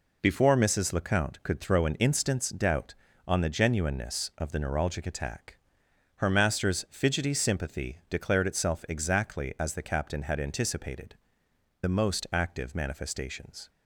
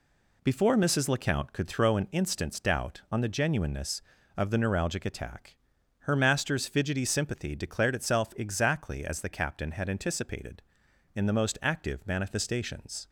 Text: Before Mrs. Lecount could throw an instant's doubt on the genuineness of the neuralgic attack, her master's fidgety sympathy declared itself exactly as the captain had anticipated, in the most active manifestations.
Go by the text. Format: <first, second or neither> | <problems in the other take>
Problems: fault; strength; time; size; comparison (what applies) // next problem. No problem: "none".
second | skips "in"; at 11.4 s